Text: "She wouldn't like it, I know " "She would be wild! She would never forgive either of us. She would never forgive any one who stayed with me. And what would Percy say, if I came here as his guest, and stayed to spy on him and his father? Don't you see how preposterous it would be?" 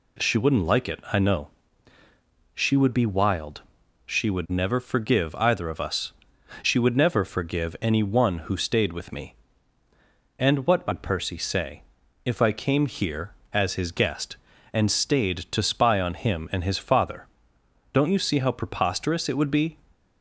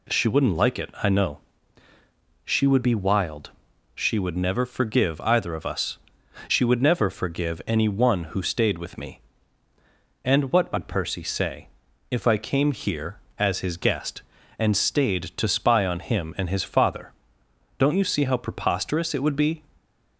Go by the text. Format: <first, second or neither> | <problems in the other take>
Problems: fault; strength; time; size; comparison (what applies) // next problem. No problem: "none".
neither | none